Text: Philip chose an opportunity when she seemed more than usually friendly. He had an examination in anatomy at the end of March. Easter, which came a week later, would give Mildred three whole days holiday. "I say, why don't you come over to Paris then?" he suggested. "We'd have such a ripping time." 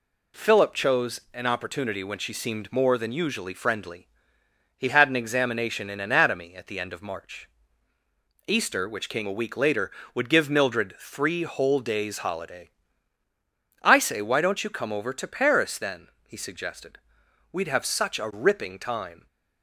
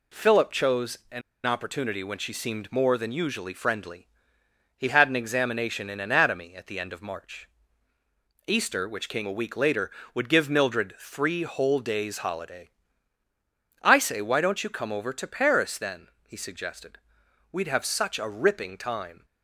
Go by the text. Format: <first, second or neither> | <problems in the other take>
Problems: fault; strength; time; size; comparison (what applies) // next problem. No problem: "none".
first | pauses between "an" and "opportunity"; slight; at 1.2 s; 0.25 s long